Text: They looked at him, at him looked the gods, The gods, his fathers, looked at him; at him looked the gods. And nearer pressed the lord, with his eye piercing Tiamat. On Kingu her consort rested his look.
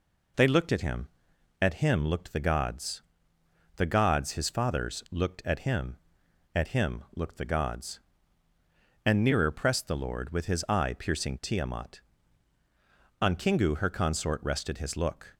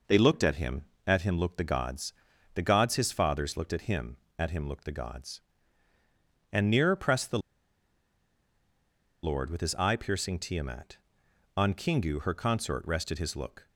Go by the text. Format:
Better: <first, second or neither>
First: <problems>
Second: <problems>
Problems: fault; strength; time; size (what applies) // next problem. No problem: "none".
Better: first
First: none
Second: pauses between "the" and "lord"; strong; at 7.3 s; 1.8 s long